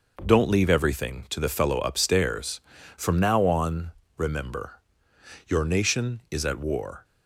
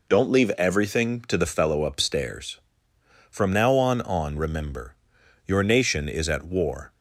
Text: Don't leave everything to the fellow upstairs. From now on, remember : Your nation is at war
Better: first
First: none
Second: says "on" twice; at 4.0 s

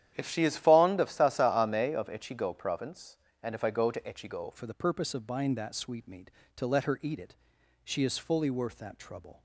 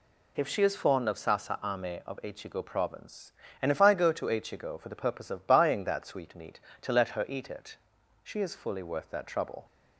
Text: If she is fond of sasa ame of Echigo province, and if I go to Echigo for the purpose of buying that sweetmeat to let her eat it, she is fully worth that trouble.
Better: second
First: starts louder than the rest; strong; until 1.1 s; 10.5 dB // changes voice at "for"; from 4.5 s on; 4.9 s long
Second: none

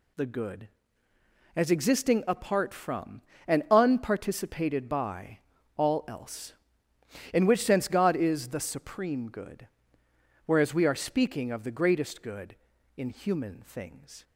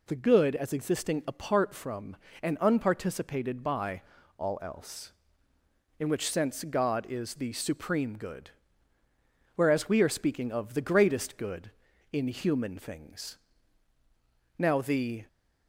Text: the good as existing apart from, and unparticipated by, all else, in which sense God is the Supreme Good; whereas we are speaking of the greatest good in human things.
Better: first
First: none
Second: goes on to say "Now the"; noticeable; from 14.5 s on; 0.70 s long

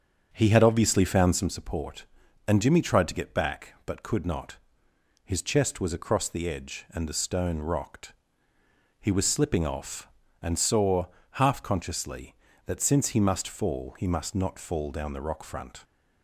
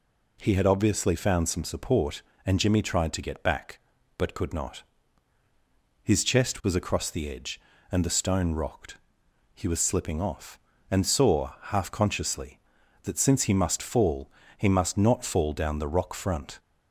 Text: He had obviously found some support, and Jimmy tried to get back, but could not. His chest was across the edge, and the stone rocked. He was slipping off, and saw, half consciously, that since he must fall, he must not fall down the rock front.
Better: second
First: starts louder than the rest; until 1.5 s; 7 dB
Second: none

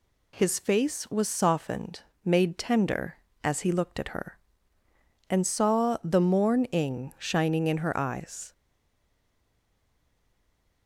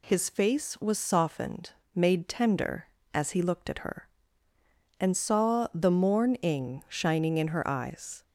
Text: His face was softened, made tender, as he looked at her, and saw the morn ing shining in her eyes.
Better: second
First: stays silent after the last word; from 8.5 s on; 2.3 s long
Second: none

